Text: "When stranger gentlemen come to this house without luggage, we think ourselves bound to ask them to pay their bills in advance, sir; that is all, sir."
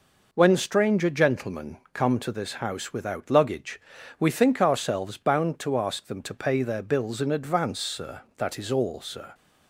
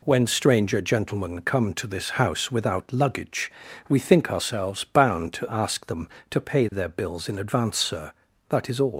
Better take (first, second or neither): first